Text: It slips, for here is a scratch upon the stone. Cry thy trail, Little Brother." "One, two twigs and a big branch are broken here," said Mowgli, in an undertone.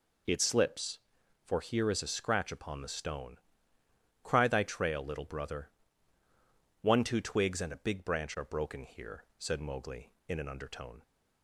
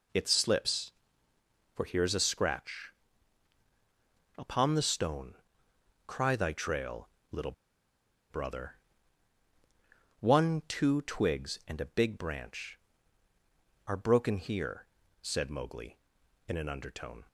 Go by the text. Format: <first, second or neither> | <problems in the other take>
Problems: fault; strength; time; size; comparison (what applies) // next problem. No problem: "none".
first | pauses between "scratch" and "upon"; strong; at 2.9 s; 1.4 s long // pauses between "Little" and "Brother"; noticeable; at 7.5 s; 0.78 s long